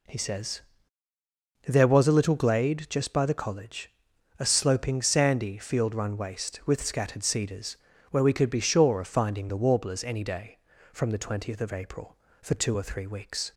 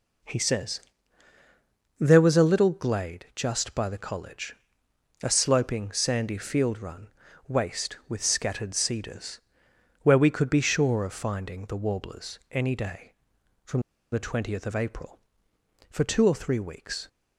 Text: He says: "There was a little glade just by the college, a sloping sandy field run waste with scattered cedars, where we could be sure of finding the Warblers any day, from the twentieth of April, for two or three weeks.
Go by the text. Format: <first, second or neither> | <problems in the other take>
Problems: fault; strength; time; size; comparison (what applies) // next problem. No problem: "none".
first | pauses between "run" and "waste"; slight; at 7.0 s; 0.36 s long // pauses between "from" and "the"; slight; at 13.8 s; 0.30 s long